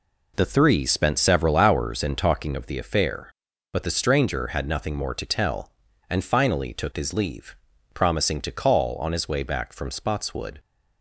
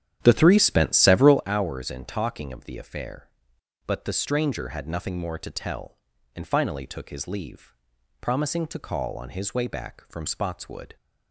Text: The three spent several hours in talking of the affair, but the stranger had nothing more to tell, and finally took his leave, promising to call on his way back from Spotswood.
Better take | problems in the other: first | starts louder than the rest; strong; until 1.4 s; 10 dB

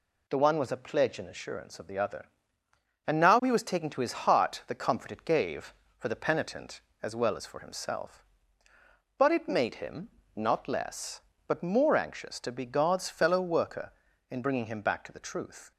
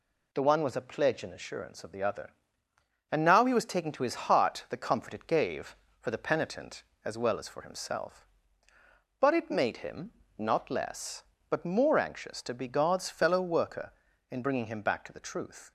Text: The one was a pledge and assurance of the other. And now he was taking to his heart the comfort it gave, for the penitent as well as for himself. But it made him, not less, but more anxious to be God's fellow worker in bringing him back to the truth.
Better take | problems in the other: neither | none

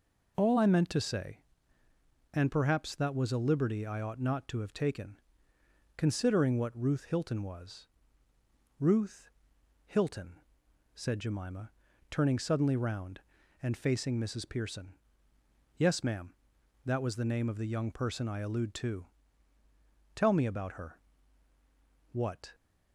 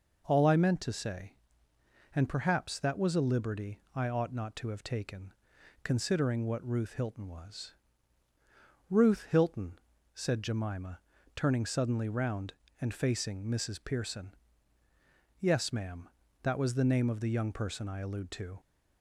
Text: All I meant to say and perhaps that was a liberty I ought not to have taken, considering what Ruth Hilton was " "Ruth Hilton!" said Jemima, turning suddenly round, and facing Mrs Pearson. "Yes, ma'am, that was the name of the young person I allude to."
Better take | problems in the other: second | pauses between "Ruth" and "Hilton"; noticeable; at 9.2 s; 0.56 s long // goes on to say "Tell me about her what"; strong; from 20.1 s on; 2.4 s long

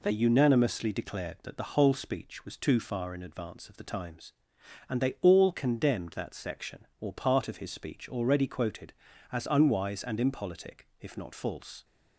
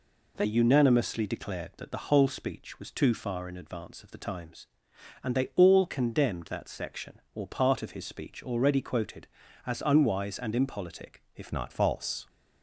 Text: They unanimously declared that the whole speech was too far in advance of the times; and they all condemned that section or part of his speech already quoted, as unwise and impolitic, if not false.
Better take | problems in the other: first | changes voice at "not"; from 11.5 s on; 0.7 s long

